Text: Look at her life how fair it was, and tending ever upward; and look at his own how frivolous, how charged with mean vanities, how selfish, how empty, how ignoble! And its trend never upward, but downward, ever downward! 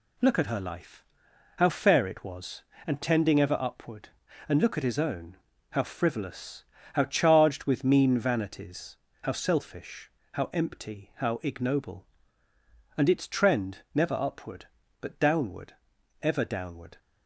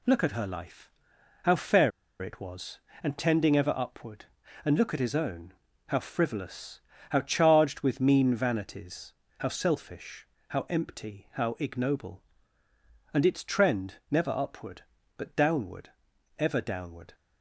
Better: first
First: pauses between "life" and "how"; noticeable; at 1.0 s; 0.56 s long // pauses between "own" and "how"; slight; at 5.3 s; 0.36 s long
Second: pauses between "life" and "how"; noticeable; at 0.8 s; 0.56 s long // pauses between "fair" and "it"; slight; at 1.9 s; 0.30 s long // pauses between "own" and "how"; slight; at 5.5 s; 0.36 s long

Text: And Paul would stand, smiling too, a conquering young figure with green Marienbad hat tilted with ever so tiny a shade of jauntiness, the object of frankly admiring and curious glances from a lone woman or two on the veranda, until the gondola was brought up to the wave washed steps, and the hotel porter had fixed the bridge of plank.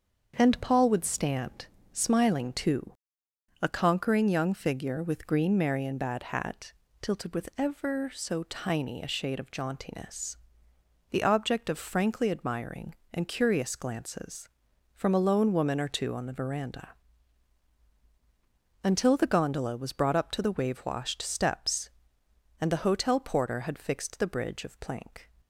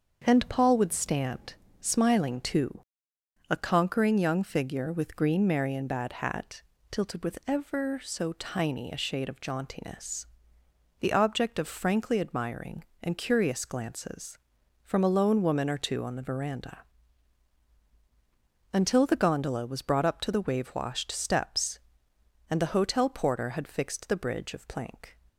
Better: neither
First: starts louder than the rest; until 1.3 s; 7 dB // pauses between "hat" and "tilted"; slight; at 6.7 s; 0.30 s long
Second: starts louder than the rest; until 1.2 s; 6.5 dB // pauses between "hat" and "tilted"; slight; at 6.6 s; 0.30 s long

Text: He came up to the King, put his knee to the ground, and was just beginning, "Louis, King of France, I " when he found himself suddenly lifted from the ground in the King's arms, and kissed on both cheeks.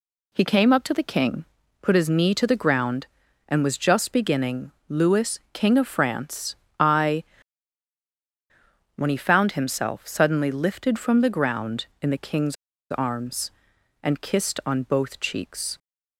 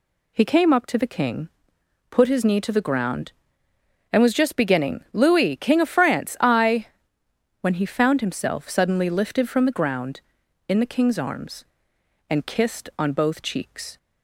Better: second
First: pauses between "King's" and "arms"; at 12.5 s; 0.36 s long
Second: none

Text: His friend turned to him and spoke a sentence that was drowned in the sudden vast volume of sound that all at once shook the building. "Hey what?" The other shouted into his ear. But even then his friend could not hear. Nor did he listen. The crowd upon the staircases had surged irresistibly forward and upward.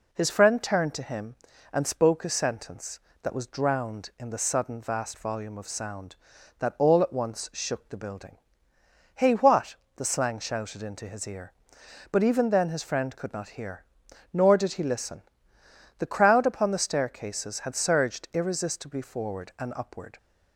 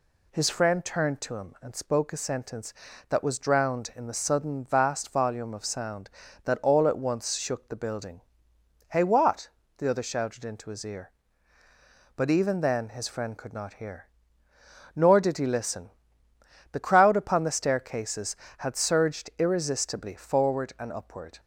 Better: second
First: says "slang" for "other"; at 10.0 s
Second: none

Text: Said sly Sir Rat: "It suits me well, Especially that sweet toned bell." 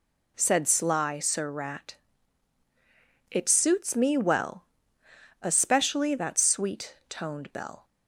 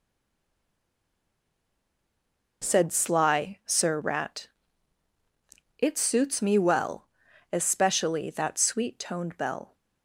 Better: first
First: none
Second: stays silent before the first word; strong; until 2.6 s; 2.6 s long

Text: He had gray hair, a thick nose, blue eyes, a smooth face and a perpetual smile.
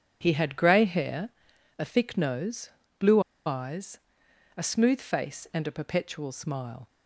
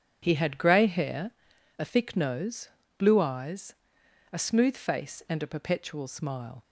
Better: second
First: pauses between "blue" and "eyes"; slight; at 3.1 s; 0.26 s long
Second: none

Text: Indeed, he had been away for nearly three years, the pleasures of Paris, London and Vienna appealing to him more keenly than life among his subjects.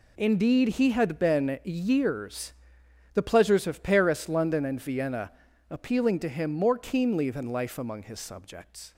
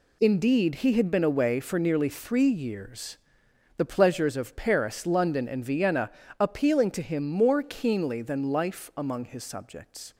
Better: second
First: skips "away for nearly three"; at 1.6 s // pauses between "Vienna" and "appealing"; at 5.3 s; 0.38 s long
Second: pauses between "Vienna" and "appealing"; slight; at 6.1 s; 0.30 s long

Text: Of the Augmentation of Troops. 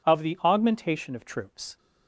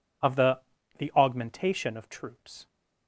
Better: first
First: none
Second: says "the" twice; at 0.9 s

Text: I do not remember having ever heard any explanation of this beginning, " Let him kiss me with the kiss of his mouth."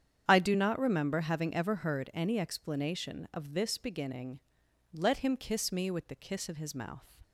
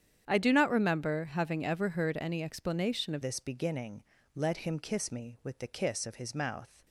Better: first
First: starts louder than the rest; strong; until 1.2 s; 9 dB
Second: starts louder than the rest; strong; until 1.2 s; 9 dB // changes voice at "this"; from 3.2 s on; 3.6 s long

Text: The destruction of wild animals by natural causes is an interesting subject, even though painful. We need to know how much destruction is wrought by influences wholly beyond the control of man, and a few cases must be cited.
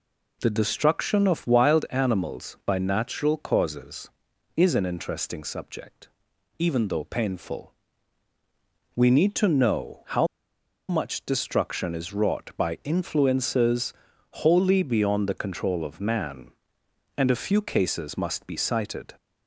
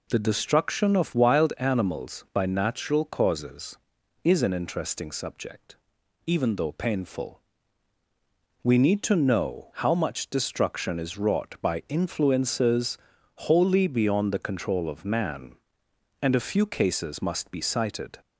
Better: second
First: pauses between "how" and "much"; noticeable; at 10.2 s; 0.62 s long // pauses between "influences" and "wholly"; noticeable; at 13.9 s; 0.50 s long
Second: pauses between "influences" and "wholly"; noticeable; at 12.9 s; 0.50 s long

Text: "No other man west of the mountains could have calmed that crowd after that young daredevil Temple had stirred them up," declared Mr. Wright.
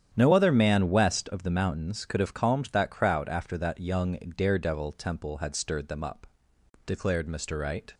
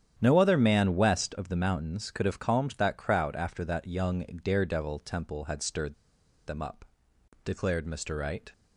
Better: first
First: starts louder than the rest; strong; until 1.1 s; 9.5 dB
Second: starts louder than the rest; strong; until 1.2 s; 10 dB // pauses between "stirred" and "them"; noticeable; at 5.9 s; 0.52 s long

